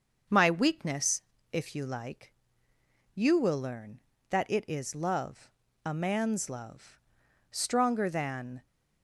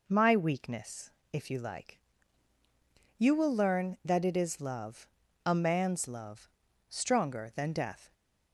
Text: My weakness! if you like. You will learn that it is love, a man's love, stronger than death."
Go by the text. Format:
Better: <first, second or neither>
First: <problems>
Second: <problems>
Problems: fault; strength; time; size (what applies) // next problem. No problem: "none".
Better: second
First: starts louder than the rest; until 1.6 s; 6.5 dB // stops before "death"; at 8.6 s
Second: none